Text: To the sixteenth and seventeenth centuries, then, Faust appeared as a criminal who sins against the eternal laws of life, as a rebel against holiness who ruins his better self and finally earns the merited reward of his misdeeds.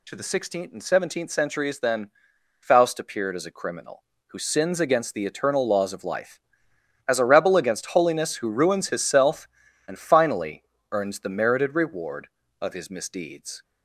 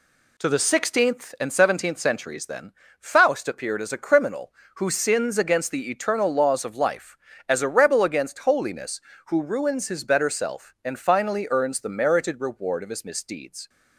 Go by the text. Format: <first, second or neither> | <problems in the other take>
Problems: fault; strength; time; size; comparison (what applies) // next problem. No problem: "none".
second | skips "better"; at 9.0 s // pauses between "finally" and "earns"; slight; at 10.6 s; 0.26 s long